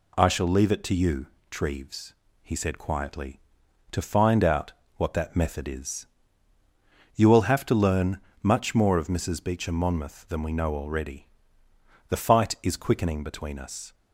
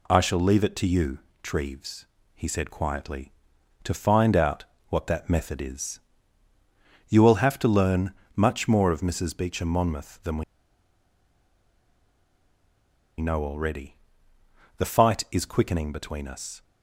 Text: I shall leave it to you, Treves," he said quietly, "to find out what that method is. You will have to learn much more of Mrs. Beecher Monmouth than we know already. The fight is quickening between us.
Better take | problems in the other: first | pauses between "out" and "what"; slight; at 4.6 s; 0.24 s long; slight in the first // pauses between "learn" and "much"; slight; at 8.1 s; 0.24 s long; slight in the first // pauses between "we" and "know"; strong; at 10.4 s; 2.7 s long

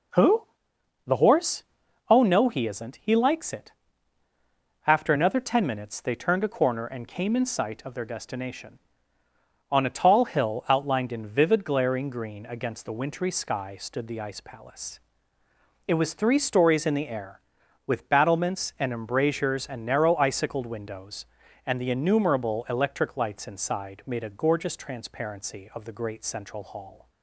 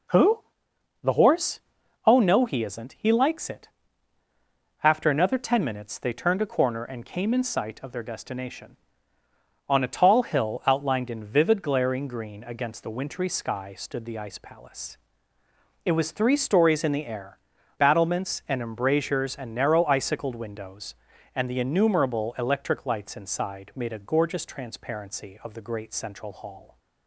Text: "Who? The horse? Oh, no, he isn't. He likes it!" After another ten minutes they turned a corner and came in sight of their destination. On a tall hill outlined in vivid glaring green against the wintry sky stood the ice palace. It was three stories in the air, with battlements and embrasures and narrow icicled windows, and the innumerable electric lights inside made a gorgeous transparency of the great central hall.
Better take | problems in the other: first | skips "with"; at 17.5 s

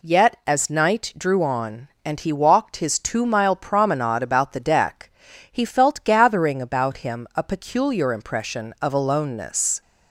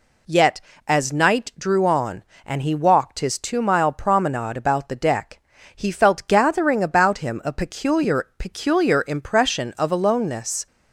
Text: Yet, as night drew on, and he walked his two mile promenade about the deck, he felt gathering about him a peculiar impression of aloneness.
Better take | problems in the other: first | says "peculiar" twice; at 8.3 s

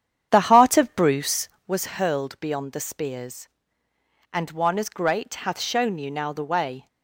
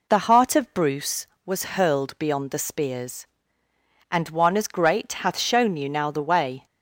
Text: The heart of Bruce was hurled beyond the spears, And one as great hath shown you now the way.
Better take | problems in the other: second | starts louder than the rest; strong; until 1.9 s; 9 dB

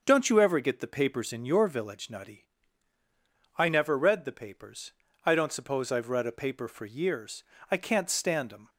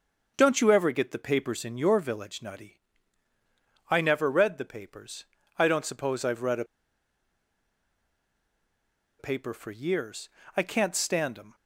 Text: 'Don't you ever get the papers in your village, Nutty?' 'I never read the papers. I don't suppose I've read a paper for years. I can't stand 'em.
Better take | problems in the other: first | starts louder than the rest; until 1.3 s; 6.5 dB; also in the first // pauses between "a" and "paper"; strong; at 6.6 s; 2.5 s long

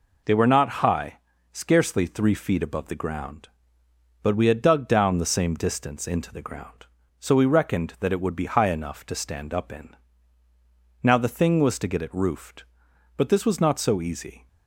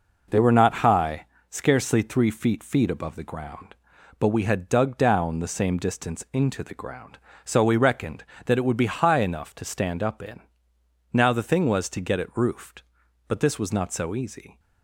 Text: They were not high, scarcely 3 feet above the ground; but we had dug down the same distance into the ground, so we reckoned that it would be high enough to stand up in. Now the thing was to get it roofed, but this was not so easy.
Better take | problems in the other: first | says "feet" twice; at 2.6 s

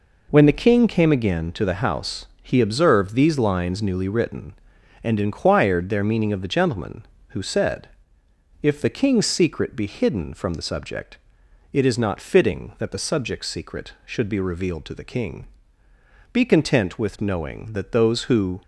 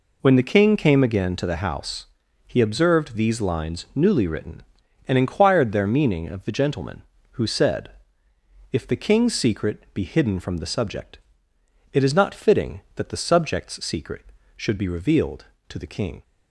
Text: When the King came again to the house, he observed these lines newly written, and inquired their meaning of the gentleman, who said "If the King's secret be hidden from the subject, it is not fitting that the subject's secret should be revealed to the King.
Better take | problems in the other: second | pauses between "said" and "If"; noticeable; at 7.8 s; 0.74 s long; noticeable in the second // goes on to say "Be content with knowing that those who"; strong; from 16.3 s on; 2.3 s long

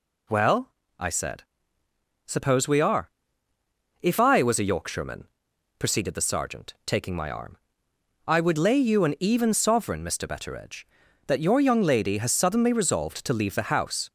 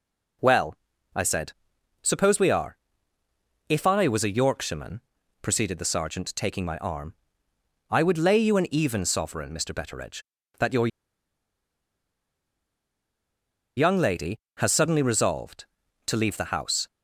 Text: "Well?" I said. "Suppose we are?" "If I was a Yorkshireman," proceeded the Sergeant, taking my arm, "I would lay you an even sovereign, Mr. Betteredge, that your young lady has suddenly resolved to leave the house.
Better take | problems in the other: first | pauses between "your" and "young"; strong; at 10.8 s; 2.8 s long

